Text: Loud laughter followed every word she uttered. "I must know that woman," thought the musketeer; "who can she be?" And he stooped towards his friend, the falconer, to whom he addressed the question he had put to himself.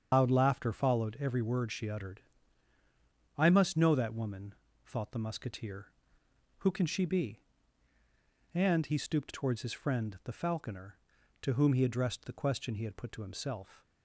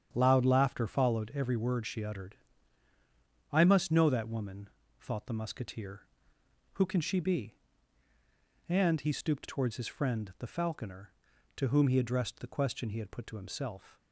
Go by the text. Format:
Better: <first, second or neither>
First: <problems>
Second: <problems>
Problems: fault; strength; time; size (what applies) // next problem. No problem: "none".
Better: second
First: loses the start of "Loud"; at 0.1 s; 160 ms // starts louder than the rest; strong; until 1.1 s; 8 dB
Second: starts louder than the rest; strong; until 1.1 s; 8.5 dB